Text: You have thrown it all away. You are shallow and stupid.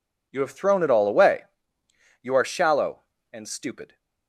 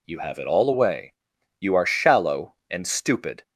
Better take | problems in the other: first | skips "thrown"; at 0.3 s

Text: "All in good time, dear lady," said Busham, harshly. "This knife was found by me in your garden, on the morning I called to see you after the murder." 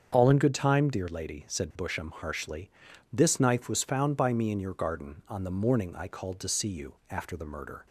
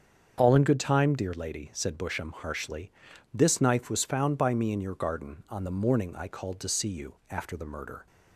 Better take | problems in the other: neither | starts louder than the rest; strong; the same in both

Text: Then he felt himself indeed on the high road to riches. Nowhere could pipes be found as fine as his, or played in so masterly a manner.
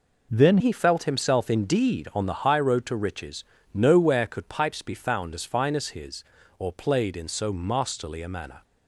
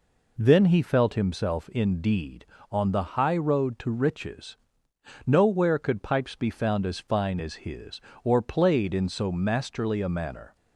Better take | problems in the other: second | changes voice at "he"; from 0.6 s on; 8.0 s long

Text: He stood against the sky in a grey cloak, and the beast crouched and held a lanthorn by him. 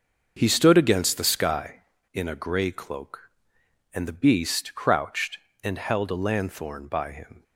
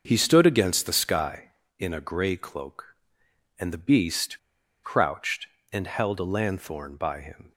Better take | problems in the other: first | starts louder than the rest; until 1.0 s; 6.5 dB; also in the first // pauses between "beast" and "crouched"; at 4.3 s; 0.45 s long

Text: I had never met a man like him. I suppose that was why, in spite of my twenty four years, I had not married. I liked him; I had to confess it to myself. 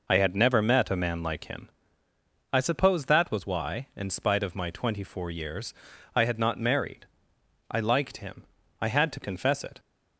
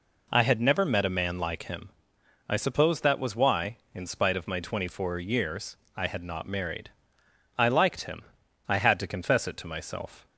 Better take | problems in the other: second | stops before "to myself"; at 9.7 s

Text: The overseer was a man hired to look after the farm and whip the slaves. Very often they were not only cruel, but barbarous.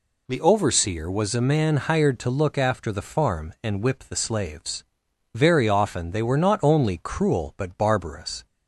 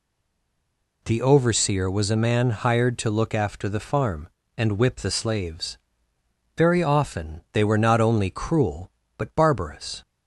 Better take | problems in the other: first | stays silent before the first word; until 1.0 s; 1.0 s long

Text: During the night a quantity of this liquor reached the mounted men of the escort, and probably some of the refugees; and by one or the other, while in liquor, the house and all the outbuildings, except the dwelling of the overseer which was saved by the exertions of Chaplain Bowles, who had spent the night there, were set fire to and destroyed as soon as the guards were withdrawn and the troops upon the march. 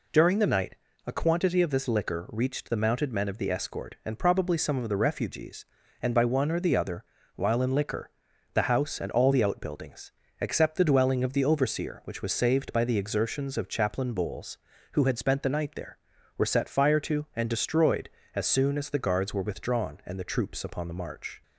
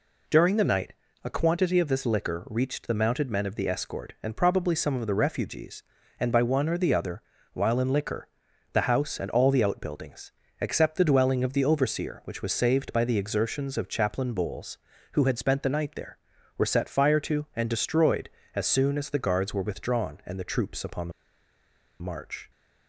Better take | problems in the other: first | pauses between "night" and "a"; slight; at 0.9 s; 0.30 s long; slight in the first // pauses between "the" and "march"; noticeable; at 21.1 s; 0.90 s long

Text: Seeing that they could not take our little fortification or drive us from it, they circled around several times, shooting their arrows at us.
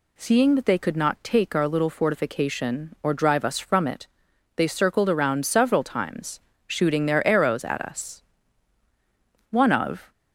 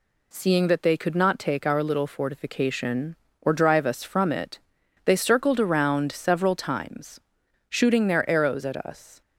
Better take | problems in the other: second | goes on to say "One of"; from 9.5 s on; 0.60 s long

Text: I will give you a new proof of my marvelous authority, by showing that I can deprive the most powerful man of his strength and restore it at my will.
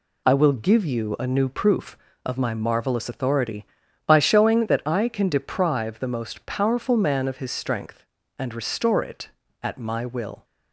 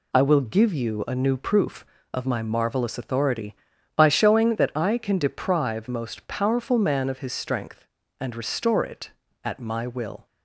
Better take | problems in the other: first | skips "the"; at 5.8 s

